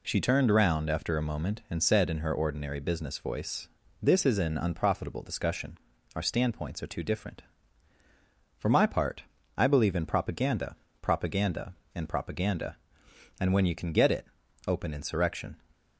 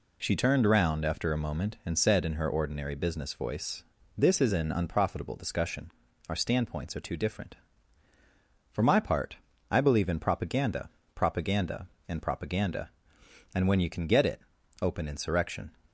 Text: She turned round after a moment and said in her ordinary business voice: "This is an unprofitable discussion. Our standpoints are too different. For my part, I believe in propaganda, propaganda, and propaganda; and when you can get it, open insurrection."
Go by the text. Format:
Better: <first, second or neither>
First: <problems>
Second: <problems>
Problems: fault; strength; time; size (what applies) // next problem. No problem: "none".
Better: neither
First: none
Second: none